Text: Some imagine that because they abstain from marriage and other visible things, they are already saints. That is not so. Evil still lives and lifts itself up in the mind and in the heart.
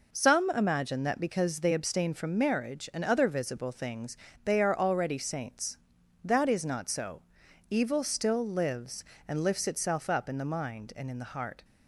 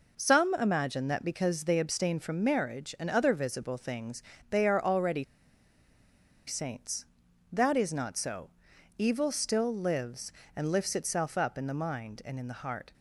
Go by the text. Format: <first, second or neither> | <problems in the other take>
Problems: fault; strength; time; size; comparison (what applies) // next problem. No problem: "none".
first | pauses between "already" and "saints"; at 5.2 s; 1.2 s long